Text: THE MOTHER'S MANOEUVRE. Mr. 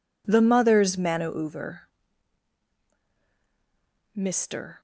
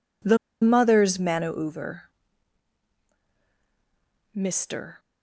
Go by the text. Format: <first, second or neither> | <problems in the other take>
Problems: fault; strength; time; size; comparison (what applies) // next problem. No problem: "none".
first | pauses between "THE" and "MOTHER'S"; slight; at 0.3 s; 0.25 s long